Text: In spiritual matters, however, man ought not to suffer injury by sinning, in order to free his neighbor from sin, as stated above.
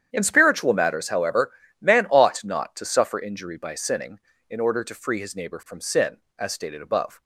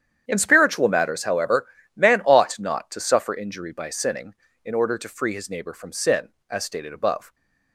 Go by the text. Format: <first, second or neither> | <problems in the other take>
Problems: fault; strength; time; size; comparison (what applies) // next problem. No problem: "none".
neither | starts louder than the rest; strong; the same in both